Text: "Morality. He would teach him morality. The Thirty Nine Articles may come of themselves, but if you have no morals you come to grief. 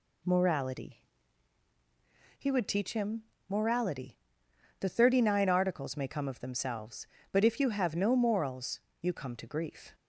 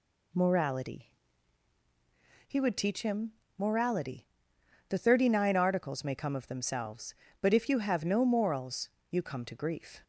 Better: neither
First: pauses between "him" and "morality"; slight; at 3.2 s; 0.26 s long // pauses between "morals" and "you"; slight; at 8.8 s; 0.20 s long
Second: pauses between "him" and "morality"; slight; at 3.3 s; 0.26 s long // pauses between "morals" and "you"; slight; at 8.8 s; 0.20 s long

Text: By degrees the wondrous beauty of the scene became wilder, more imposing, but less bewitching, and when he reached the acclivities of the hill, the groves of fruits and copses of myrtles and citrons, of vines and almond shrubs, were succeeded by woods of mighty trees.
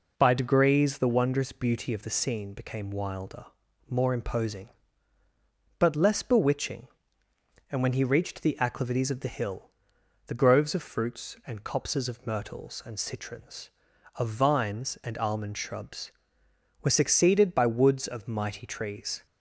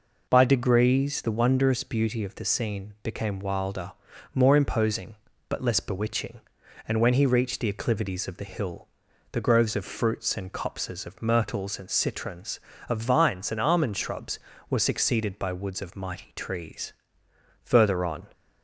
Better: first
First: none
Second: goes on to say "Further on"; noticeable; from 17.6 s on; 0.62 s long

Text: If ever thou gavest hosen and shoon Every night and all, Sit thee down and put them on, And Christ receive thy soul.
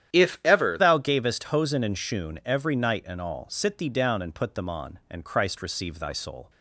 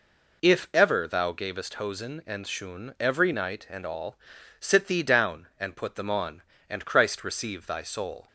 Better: second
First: starts louder than the rest; strong; until 1.2 s; 10.5 dB // changes voice at "thou"; from 0.7 s on; 5.7 s long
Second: none

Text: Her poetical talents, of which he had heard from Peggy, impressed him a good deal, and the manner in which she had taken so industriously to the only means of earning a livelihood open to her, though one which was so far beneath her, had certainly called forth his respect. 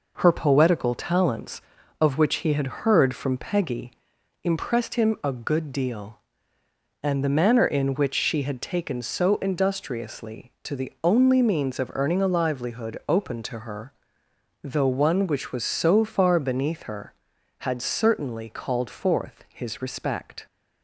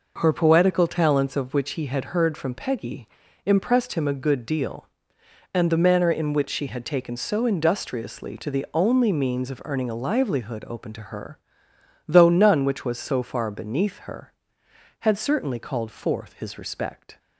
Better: first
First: none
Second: says "none" for "one"; at 12.3 s

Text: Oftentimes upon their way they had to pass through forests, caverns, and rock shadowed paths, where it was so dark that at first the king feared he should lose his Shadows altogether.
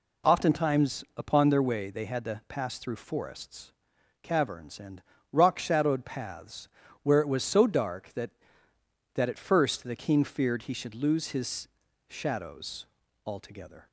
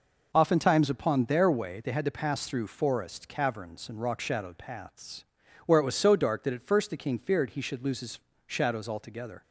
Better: second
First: pauses between "and" and "rock"; slight; at 5.0 s; 0.28 s long // says "that" twice; at 9.1 s // pauses between "his" and "Shadows"; at 11.6 s; 0.38 s long // pauses between "Shadows" and "altogether"; at 12.8 s; 0.40 s long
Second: pauses between "his" and "Shadows"; slight; at 8.1 s; 0.32 s long

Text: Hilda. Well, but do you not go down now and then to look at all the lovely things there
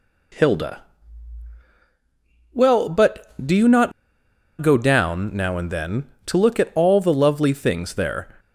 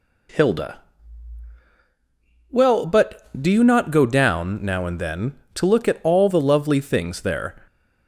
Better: second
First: pauses between "not" and "go"; noticeable; at 3.9 s; 0.70 s long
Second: none

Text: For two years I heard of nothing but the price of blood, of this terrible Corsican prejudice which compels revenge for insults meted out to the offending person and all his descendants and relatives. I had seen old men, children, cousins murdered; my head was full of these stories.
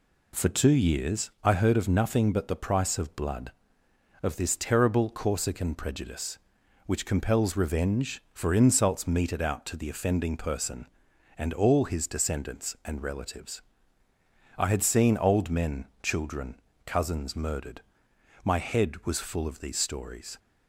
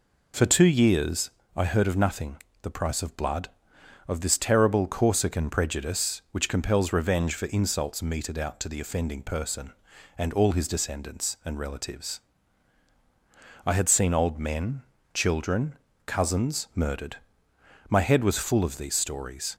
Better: first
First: none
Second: pauses between "years" and "I"; slight; at 1.3 s; 0.24 s long // skips "but"; at 2.5 s

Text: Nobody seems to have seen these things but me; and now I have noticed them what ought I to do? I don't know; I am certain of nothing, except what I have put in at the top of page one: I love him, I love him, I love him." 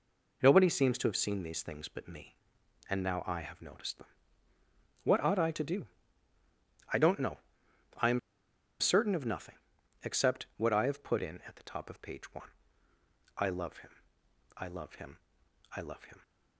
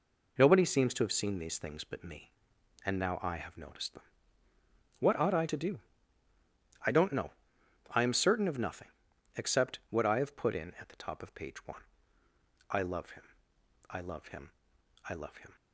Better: second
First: pauses between "them" and "what"; noticeable; at 4.0 s; 0.98 s long // pauses between "am" and "certain"; noticeable; at 8.1 s; 0.60 s long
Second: pauses between "them" and "what"; noticeable; at 4.0 s; 0.98 s long

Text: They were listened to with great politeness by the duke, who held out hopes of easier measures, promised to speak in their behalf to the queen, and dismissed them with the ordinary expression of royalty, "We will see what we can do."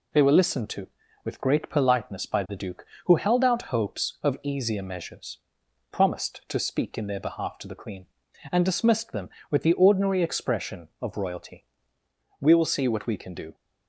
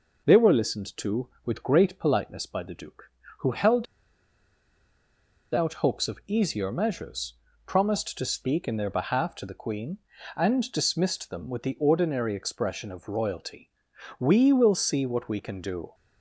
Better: first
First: none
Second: pauses between "held" and "out"; strong; at 3.8 s; 1.6 s long

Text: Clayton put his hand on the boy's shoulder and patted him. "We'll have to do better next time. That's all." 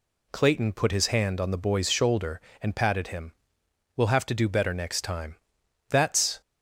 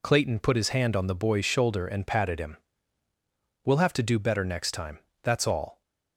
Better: second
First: stops before "all"; at 6.4 s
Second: none

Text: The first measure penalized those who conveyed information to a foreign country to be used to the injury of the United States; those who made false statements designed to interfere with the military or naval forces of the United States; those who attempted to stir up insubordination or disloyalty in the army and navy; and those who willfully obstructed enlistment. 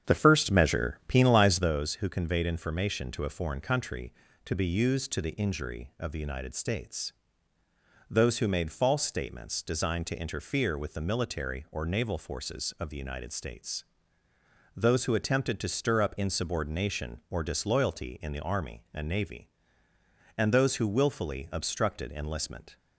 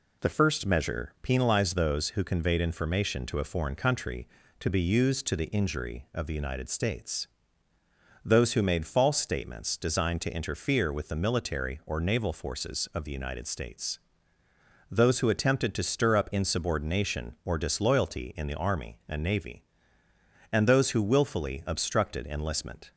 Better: second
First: starts louder than the rest; strong; until 1.7 s; 8 dB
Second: none

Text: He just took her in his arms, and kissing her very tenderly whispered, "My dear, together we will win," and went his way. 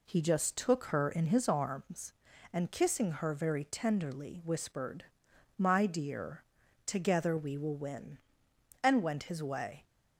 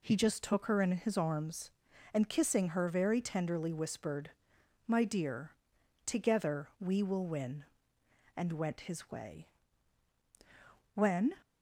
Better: first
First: none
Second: goes on to say "When"; slight; from 10.9 s on; 0.40 s long

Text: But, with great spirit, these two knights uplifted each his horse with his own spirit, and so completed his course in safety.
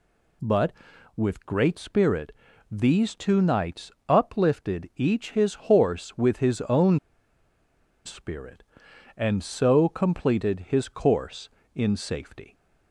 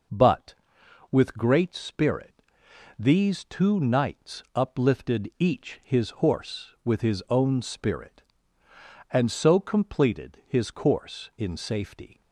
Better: second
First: pauses between "knights" and "uplifted"; slight; at 3.9 s; 0.16 s long // pauses between "own" and "spirit"; at 6.9 s; 1.0 s long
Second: none

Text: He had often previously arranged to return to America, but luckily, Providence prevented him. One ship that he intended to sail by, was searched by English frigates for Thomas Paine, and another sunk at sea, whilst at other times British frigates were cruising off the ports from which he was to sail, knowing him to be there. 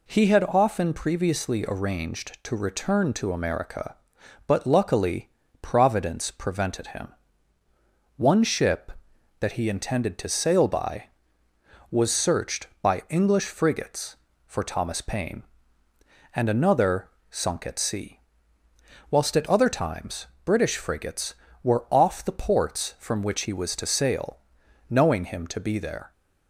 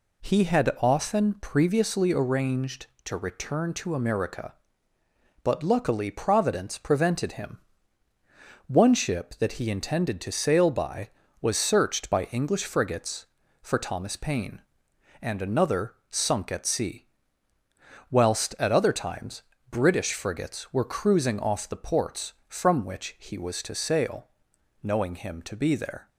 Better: second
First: pauses between "another" and "sunk"; slight; at 17.0 s; 0.22 s long // pauses between "times" and "British"; slight; at 20.2 s; 0.18 s long // skips "cruising"; at 21.8 s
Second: pauses between "times" and "British"; slight; at 19.4 s; 0.28 s long

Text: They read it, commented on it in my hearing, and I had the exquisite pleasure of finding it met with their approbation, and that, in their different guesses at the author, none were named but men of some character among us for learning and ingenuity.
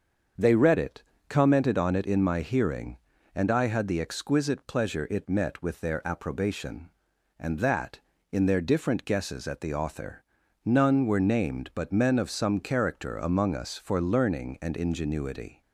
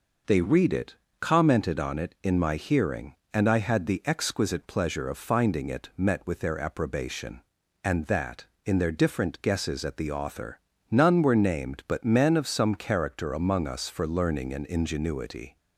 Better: second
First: starts louder than the rest; until 1.6 s; 7 dB // skips "of finding"; at 5.0 s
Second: none

